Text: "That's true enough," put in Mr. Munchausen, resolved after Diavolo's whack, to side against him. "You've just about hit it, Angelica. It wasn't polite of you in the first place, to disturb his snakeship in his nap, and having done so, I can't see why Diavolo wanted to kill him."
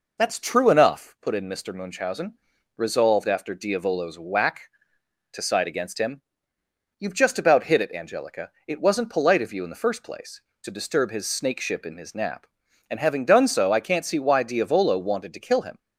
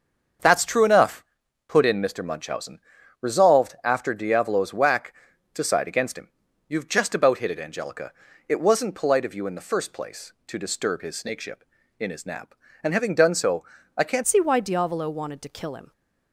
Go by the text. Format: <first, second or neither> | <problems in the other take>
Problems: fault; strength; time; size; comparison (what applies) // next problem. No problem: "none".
first | starts louder than the rest; until 1.8 s; 6.5 dB // changes voice at "see"; from 14.2 s on; 1.7 s long